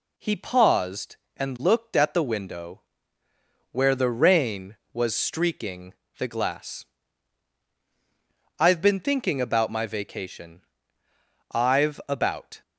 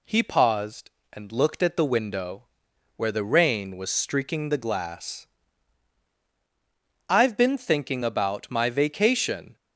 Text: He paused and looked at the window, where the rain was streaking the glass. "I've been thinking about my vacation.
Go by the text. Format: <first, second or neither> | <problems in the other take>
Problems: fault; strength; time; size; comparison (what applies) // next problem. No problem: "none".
second | pauses between "streaking" and "the"; slight; at 5.9 s; 0.24 s long // goes on to say "I've about"; noticeable; from 11.5 s on; 1.1 s long